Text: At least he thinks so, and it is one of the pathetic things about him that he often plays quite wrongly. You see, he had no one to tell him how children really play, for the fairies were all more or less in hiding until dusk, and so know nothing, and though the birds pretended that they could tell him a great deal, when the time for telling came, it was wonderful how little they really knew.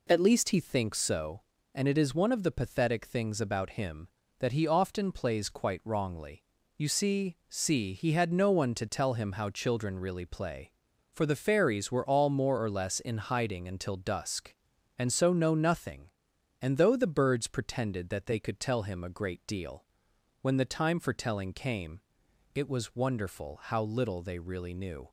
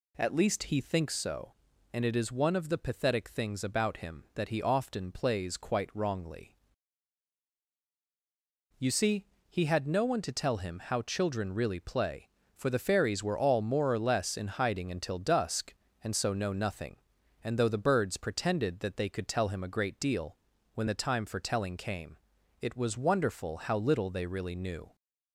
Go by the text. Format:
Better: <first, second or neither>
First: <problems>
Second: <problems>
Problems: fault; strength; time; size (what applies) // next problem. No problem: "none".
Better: second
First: says "see" twice; at 7.4 s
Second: none